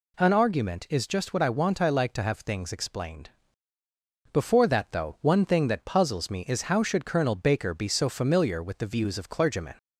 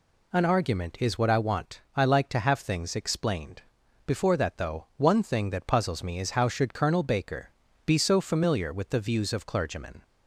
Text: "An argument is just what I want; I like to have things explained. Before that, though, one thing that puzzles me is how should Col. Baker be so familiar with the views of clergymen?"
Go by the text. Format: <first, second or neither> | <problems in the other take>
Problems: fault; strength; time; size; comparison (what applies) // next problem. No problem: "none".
first | skips "just"; at 1.1 s // pauses between "Baker" and "be"; slight; at 7.5 s; 0.36 s long